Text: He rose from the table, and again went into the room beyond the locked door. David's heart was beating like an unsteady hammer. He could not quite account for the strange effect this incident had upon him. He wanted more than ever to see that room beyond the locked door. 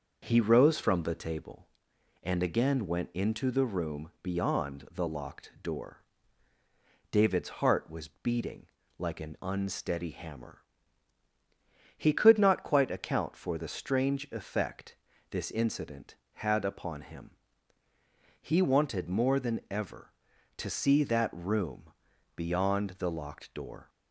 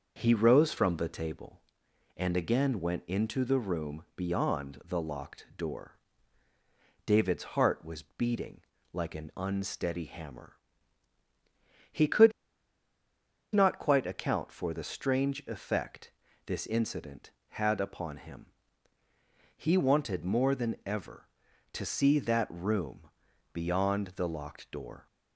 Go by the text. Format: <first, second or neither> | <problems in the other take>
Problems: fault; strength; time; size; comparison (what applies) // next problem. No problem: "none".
first | starts louder than the rest; until 1.1 s; 6.5 dB; also in the first // pauses between "beating" and "like"; slight; at 8.6 s; 0.32 s long; slight in the first // pauses between "could" and "not"; at 12.3 s; 1.2 s long // pauses between "effect" and "this"; slight; at 16.0 s; 0.36 s long; slight in the first // pauses between "room" and "beyond"; at 23.0 s; 0.42 s long; also in the first